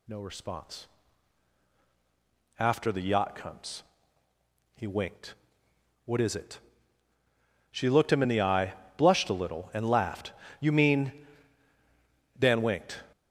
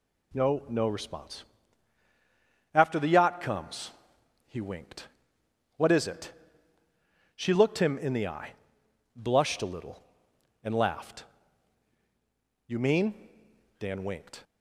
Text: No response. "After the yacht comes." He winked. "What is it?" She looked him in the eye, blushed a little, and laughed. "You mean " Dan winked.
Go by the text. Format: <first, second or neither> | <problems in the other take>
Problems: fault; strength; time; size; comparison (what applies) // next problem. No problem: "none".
first | says "No" twice; at 0.6 s